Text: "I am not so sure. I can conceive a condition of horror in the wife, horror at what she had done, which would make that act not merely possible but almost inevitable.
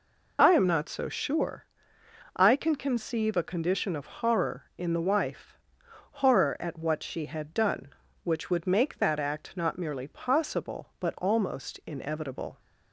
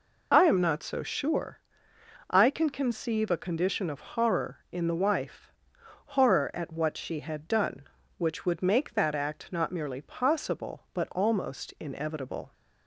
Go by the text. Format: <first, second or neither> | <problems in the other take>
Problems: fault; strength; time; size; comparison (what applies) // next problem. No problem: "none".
neither | none